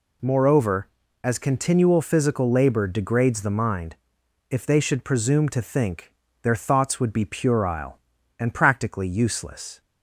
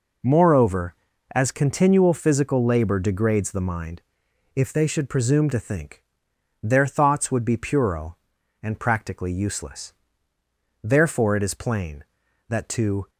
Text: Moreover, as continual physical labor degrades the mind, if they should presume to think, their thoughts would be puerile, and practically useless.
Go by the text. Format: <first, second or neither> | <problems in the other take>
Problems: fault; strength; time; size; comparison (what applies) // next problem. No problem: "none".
first | goes on to say "Therefore it is plain that to"; strong; from 10.8 s on; 2.2 s long